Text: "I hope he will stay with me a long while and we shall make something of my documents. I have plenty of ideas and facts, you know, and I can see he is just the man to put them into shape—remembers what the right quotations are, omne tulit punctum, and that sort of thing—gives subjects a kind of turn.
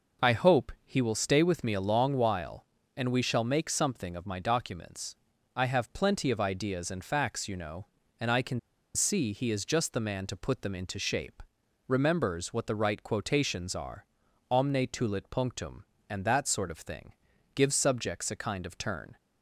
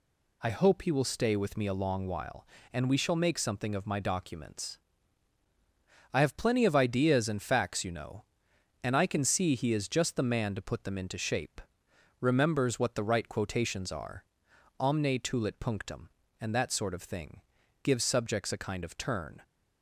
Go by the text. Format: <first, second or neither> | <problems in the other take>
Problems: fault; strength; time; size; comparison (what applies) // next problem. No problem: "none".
second | pauses between "can" and "see"; slight; at 8.5 s; 0.35 s long